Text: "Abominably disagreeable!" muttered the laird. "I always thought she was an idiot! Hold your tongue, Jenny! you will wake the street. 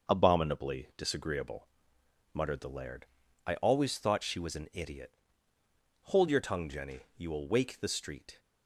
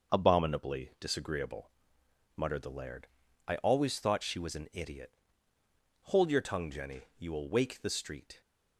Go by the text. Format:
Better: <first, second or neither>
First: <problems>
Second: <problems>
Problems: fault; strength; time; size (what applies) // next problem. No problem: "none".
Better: neither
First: starts louder than the rest; noticeable; until 1.1 s; 6 dB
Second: starts louder than the rest; noticeable; until 1.2 s; 6 dB